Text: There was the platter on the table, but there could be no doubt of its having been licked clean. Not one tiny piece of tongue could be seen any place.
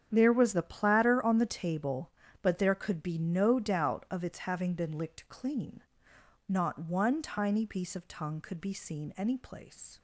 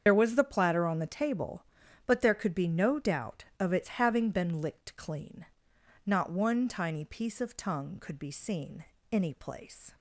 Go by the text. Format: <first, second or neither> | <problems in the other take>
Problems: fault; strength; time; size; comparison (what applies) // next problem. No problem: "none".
first | loses the start of "There"; at 0.0 s; 55 ms // starts louder than the rest; strong; until 1.0 s; 7.5 dB; strong in the first // pauses between "seen" and "any"; slight; at 8.8 s; 0.26 s long